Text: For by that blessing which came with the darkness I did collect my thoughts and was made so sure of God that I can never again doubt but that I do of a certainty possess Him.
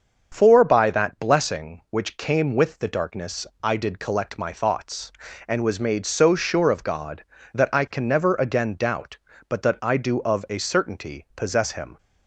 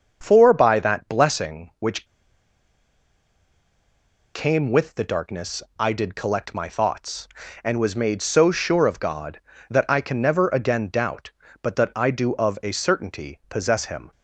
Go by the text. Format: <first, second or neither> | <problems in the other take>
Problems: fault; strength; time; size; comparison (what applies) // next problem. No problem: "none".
first | starts louder than the rest; until 1.2 s; 7 dB; also in the first // pauses between "which" and "came"; strong; at 2.0 s; 2.2 s long // pauses between "darkness" and "I"; slight; at 5.6 s; 0.18 s long; slight in the first